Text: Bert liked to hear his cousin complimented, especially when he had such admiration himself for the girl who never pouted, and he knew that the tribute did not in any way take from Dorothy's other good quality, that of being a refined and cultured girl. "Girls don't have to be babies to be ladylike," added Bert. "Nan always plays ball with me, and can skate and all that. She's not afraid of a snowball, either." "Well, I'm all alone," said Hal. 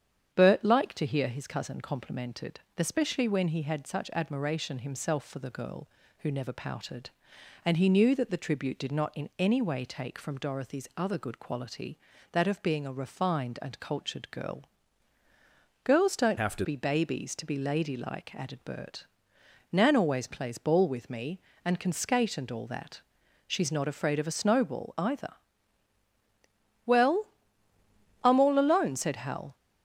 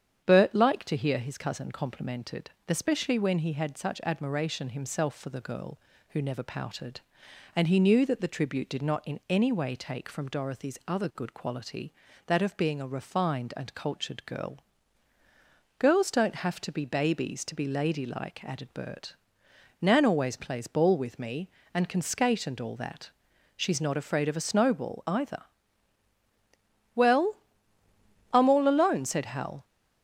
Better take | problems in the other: second | starts louder than the rest; strong; until 1.3 s; 8.5 dB; strong in the second // changes voice from "have" to "to"; from 16.3 to 16.6 s; 0.3 s long

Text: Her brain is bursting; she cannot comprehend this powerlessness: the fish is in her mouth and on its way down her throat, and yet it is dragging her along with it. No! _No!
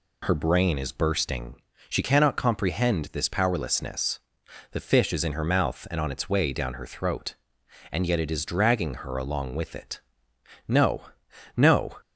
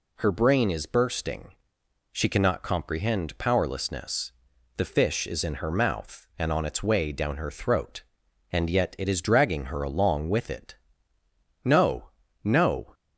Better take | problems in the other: first | skips "this"; at 3.3 s

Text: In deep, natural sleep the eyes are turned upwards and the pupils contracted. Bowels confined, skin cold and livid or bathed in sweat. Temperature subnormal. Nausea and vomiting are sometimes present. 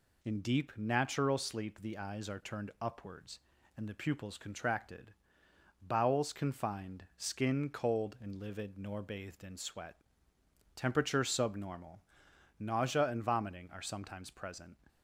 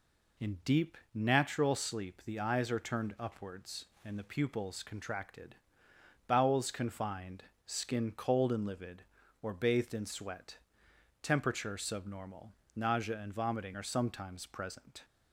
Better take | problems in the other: second | says "nor" for "or"; at 8.7 s

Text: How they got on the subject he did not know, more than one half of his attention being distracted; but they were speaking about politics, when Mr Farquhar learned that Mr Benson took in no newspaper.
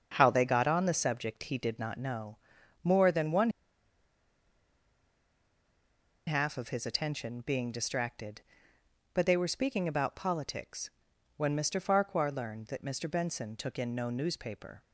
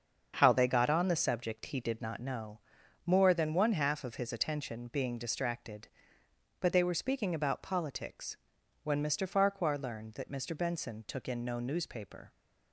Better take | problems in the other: second | starts louder than the rest; until 1.1 s; 7 dB; also in the second // pauses between "one" and "half"; strong; at 3.4 s; 2.7 s long

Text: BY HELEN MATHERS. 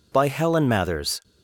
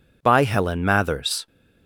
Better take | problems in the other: neither | none

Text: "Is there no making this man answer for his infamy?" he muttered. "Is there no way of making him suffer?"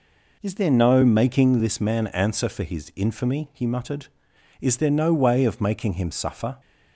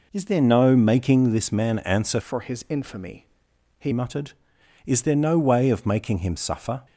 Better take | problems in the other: first | changes voice from "for" to "he"; from 2.2 to 3.9 s; 1.7 s long

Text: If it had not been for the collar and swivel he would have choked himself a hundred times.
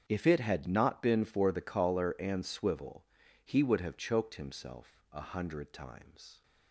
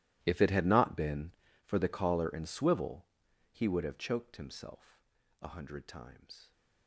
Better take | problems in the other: first | gets quieter; strong; throughout; 20.5 dB // starts louder than the rest; strong; until 1.2 s; 14.5 dB; strong in the first // pauses between "swivel" and "he"; at 3.0 s; 0.44 s long; also in the first // pauses between "himself" and "a"; at 5.0 s; 0.38 s long

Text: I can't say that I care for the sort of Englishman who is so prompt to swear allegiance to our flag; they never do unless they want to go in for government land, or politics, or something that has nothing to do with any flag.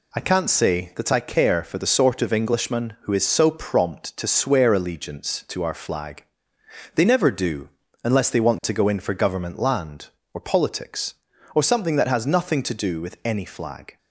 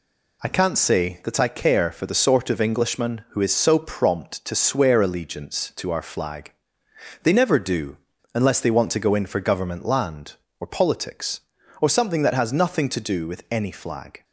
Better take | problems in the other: neither | pauses between "do" and "unless"; the same in both

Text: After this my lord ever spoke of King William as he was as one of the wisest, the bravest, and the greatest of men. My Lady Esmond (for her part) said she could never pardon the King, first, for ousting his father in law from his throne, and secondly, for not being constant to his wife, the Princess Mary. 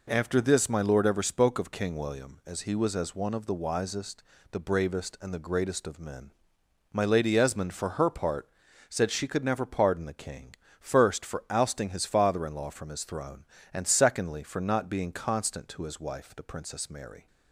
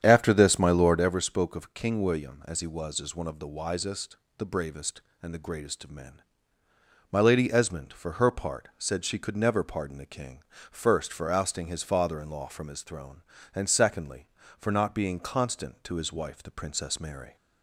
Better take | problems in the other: first | starts louder than the rest; strong; until 1.3 s; 8.5 dB

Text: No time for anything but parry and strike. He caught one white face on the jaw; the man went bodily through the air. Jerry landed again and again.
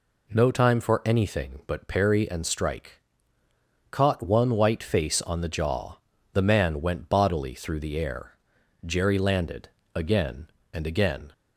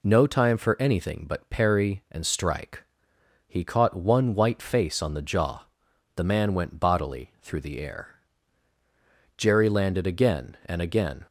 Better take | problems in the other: second | skips "He"; at 3.4 s // pauses between "landed" and "again"; slight; at 9.7 s; 0.24 s long

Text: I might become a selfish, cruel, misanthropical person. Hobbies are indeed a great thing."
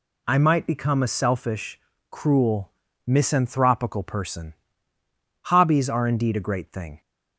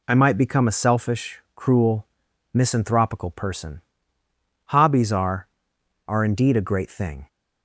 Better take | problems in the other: first | says "are" twice; at 6.0 s

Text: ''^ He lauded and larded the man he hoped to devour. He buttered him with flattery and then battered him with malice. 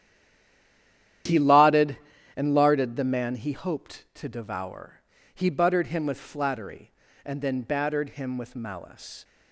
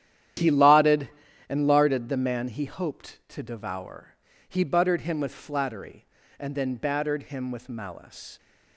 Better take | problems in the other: second | stays silent before the first word; noticeable; until 1.2 s; 1.2 s long // starts louder than the rest; strong; until 2.6 s; 11 dB; strong in the second

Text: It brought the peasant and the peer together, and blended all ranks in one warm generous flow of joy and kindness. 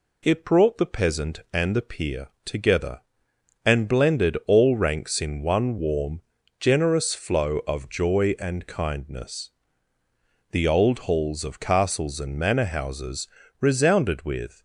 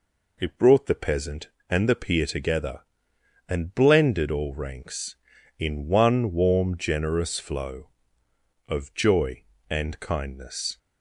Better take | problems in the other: second | pauses between "peer" and "together"; slight; at 2.2 s; 0.18 s long // pauses between "warm" and "generous"; at 6.2 s; 0.40 s long // goes on to say "The old halls of castles and manor houses resounded with"; strong; from 10.5 s on; 4.1 s long

